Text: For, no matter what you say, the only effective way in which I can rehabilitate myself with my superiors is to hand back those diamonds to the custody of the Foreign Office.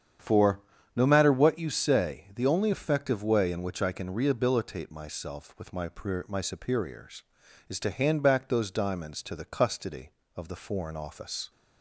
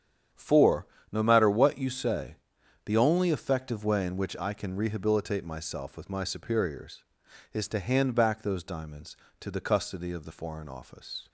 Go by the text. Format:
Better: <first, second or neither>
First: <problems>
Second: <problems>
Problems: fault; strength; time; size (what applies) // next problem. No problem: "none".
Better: second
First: starts louder than the rest; strong; until 1.5 s; 8.5 dB // says "my" twice; at 6.2 s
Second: starts louder than the rest; strong; until 1.5 s; 8.5 dB